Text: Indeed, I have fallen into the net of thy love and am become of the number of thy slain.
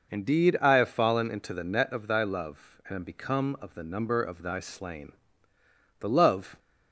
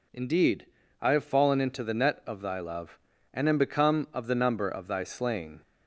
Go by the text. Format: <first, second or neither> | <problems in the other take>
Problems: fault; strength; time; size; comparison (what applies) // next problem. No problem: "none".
second | goes on to say "The love"; from 6.0 s on; 0.58 s long